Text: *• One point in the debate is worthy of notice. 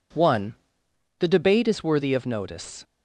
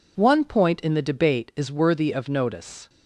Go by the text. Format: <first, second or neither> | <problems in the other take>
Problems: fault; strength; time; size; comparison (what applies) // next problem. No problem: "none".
second | skips "point in"; at 0.8 s